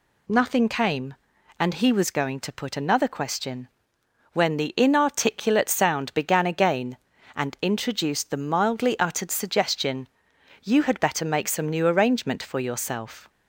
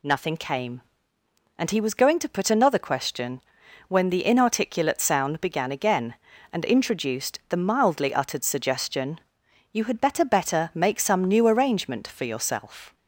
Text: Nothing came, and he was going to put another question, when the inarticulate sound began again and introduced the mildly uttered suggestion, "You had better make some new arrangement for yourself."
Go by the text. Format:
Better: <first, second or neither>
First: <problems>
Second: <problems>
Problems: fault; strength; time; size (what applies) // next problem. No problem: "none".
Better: first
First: none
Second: says "better" twice; at 10.2 s